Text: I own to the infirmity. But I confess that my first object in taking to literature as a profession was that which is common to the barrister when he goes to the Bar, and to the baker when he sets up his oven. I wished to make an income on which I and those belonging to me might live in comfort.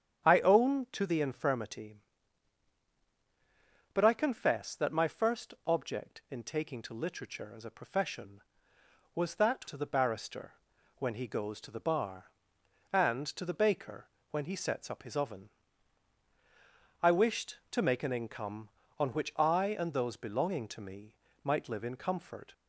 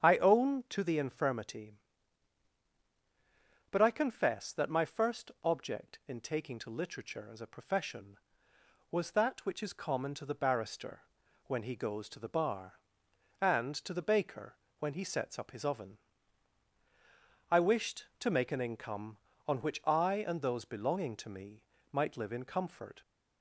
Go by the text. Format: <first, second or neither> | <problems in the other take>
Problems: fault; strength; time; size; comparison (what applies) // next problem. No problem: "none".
second | starts louder than the rest; strong; until 1.3 s; 9 dB; strong in the second // skips "which is common"; at 9.6 s // pauses between "barrister" and "when"; at 10.5 s; 0.44 s long; also in the second // pauses between "baker" and "when"; slight; at 14.0 s; 0.24 s long; slight in the second // pauses between "me" and "might"; slight; at 21.1 s; 0.28 s long; slight in the second